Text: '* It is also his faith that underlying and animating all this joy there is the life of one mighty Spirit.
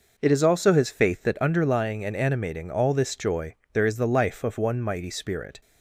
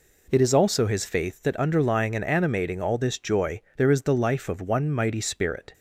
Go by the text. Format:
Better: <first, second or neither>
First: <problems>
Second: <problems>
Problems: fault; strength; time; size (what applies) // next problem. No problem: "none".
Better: neither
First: pauses between "joy" and "there"; slight; at 3.5 s; 0.20 s long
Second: pauses between "joy" and "there"; slight; at 3.6 s; 0.16 s long